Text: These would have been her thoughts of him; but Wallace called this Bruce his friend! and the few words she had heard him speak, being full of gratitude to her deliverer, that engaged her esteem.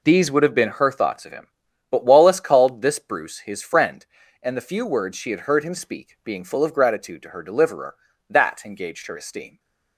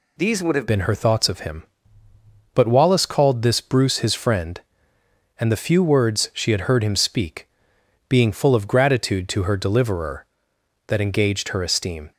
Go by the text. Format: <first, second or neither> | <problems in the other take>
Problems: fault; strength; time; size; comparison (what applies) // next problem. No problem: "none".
first | changes voice at "been"; from 0.6 s on; 11.5 s long